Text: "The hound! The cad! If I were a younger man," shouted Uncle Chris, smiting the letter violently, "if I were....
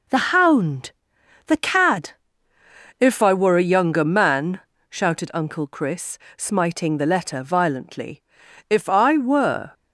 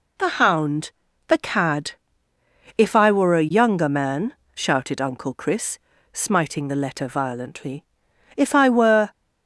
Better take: neither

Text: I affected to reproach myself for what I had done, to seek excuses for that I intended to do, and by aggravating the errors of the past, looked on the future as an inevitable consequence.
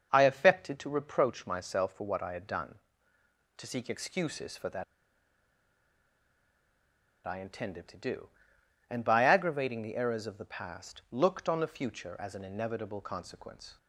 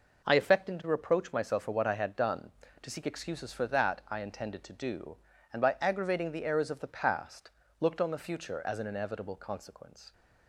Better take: second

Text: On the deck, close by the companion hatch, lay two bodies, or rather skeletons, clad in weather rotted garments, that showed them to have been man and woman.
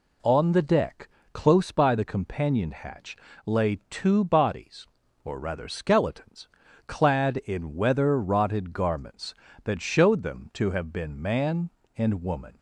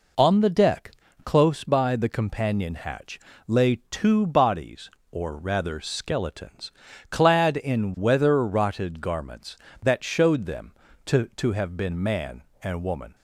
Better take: first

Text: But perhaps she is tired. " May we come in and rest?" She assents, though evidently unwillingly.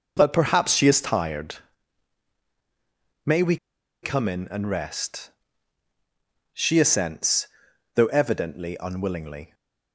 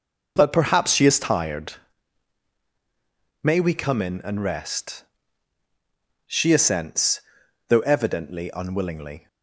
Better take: second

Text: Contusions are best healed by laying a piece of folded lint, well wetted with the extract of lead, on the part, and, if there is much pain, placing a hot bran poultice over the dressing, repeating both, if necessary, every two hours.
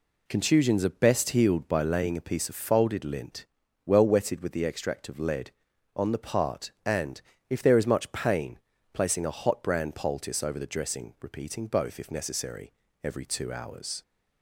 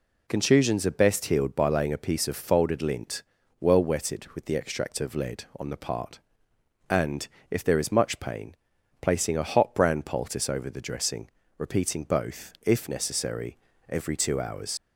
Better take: first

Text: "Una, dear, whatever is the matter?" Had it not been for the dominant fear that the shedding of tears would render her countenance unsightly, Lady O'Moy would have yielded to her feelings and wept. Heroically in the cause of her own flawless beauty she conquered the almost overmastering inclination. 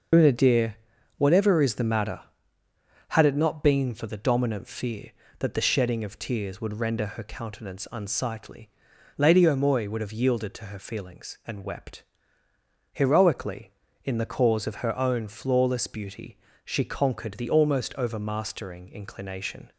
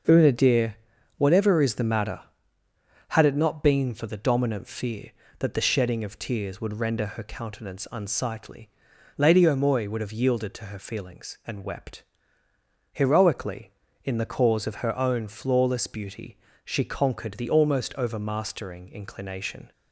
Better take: second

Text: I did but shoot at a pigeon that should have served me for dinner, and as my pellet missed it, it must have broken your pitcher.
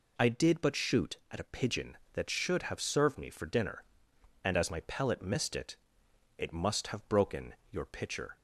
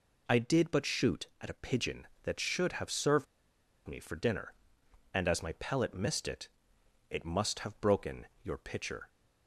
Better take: first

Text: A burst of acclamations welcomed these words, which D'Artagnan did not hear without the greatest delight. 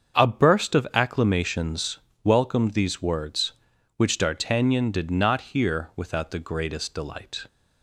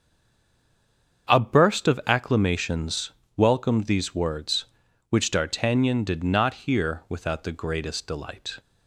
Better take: first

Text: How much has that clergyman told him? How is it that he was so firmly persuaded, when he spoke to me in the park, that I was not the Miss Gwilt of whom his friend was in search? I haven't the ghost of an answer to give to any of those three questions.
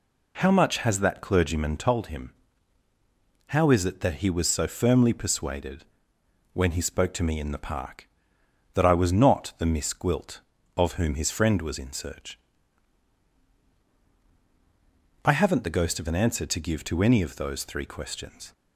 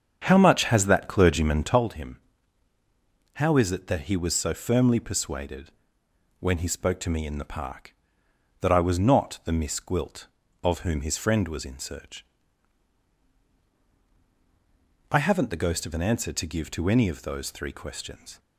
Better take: first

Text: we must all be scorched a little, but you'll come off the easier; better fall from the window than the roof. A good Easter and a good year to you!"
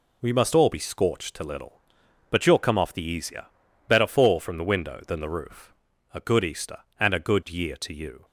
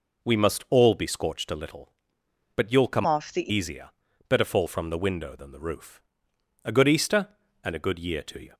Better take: first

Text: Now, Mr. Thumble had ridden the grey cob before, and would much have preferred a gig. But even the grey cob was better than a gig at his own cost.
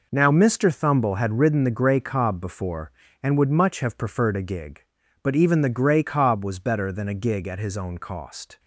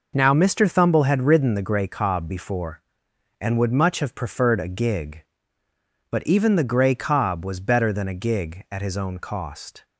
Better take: neither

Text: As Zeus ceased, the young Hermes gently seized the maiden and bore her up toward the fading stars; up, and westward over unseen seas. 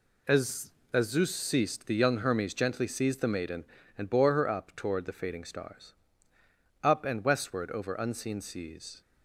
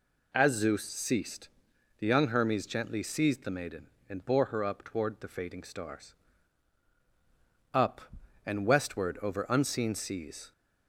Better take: second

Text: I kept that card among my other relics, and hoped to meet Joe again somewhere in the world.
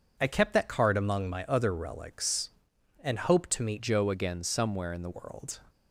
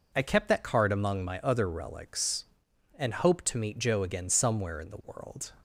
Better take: second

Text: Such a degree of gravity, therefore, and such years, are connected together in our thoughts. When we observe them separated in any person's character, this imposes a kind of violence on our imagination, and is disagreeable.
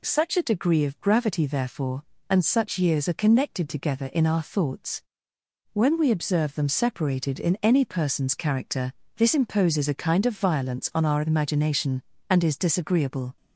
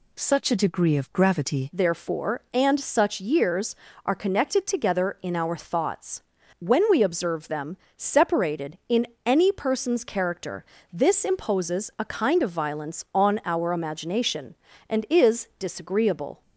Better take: first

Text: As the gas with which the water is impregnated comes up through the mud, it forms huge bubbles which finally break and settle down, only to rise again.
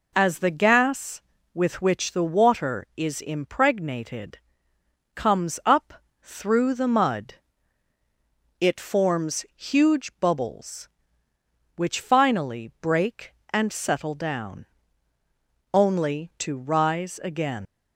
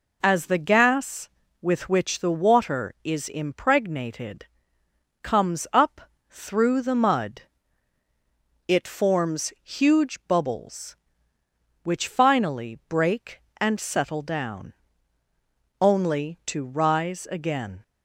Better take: second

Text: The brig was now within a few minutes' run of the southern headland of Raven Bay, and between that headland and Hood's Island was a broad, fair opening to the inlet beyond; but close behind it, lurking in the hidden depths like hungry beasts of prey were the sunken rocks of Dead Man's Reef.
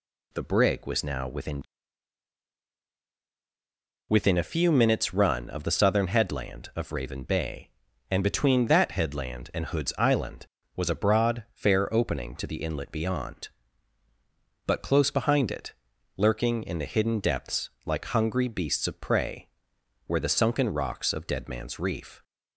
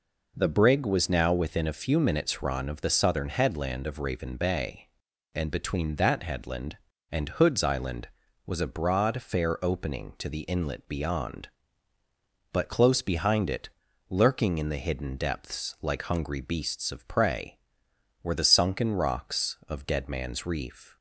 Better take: second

